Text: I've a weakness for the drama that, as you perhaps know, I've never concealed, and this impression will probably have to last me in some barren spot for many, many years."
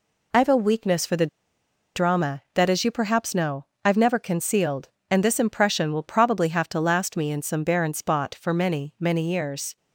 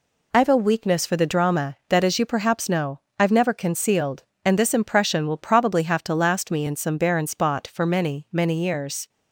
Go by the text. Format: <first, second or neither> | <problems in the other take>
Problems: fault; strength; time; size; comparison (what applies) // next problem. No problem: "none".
second | pauses between "the" and "drama"; noticeable; at 1.2 s; 0.68 s long